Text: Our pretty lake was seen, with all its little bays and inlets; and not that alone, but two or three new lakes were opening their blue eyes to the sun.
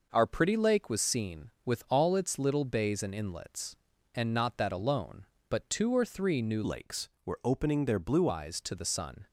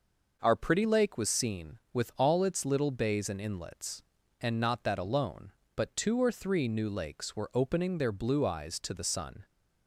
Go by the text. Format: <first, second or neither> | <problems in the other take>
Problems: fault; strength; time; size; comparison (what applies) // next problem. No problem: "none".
second | changes voice from "lakes" to "blue"; from 6.6 to 8.2 s; 1.6 s long